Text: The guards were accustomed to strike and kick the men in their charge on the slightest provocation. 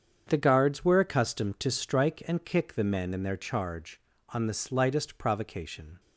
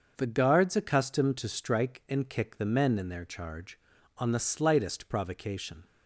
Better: first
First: starts louder than the rest; strong; until 1.2 s; 7.5 dB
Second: starts louder than the rest; until 1.1 s; 6.5 dB // skips "were"; at 0.7 s

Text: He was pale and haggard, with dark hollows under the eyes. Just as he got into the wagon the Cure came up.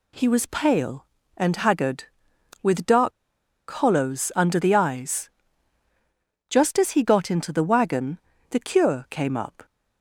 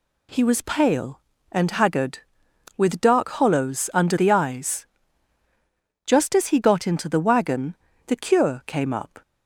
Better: second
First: pauses between "dark" and "hollows"; noticeable; at 3.1 s; 0.71 s long // pauses between "wagon" and "the"; slight; at 8.1 s; 0.32 s long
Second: pauses between "wagon" and "the"; slight; at 7.7 s; 0.32 s long

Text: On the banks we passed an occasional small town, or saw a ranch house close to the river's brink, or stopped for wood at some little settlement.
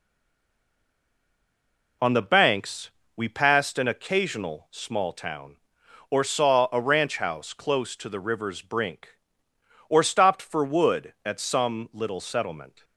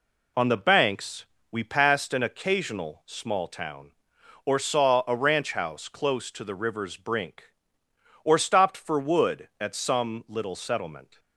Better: second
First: stays silent before the first word; noticeable; until 2.0 s; 2.0 s long // pauses between "banks" and "we"; slight; at 2.8 s; 0.24 s long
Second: pauses between "banks" and "we"; slight; at 1.2 s; 0.24 s long

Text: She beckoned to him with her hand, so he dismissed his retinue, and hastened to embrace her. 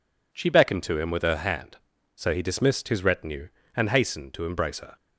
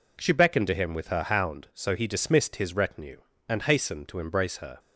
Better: first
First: none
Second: says "hound" for "hand"; at 1.2 s

